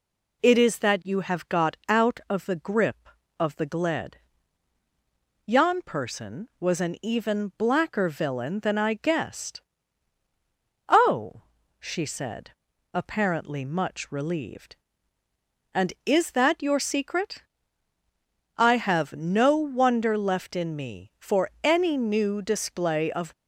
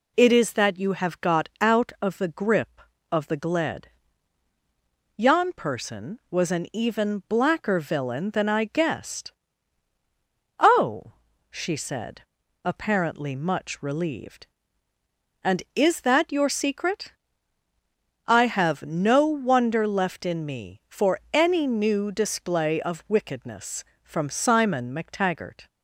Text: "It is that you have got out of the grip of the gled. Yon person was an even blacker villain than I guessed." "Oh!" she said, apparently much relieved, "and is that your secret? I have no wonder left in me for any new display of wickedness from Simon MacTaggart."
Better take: second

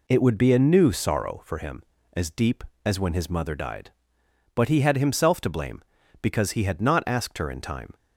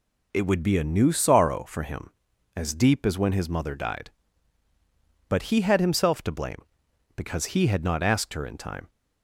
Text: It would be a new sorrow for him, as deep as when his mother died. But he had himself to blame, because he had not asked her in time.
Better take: neither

